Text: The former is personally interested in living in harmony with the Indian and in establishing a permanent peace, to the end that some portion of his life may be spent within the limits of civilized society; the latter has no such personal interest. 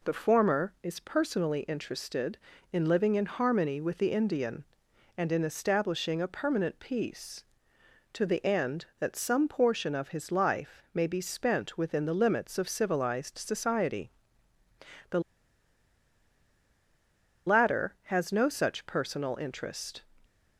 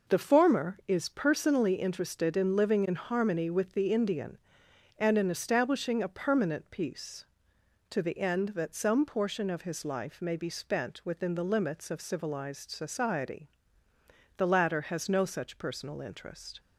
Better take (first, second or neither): second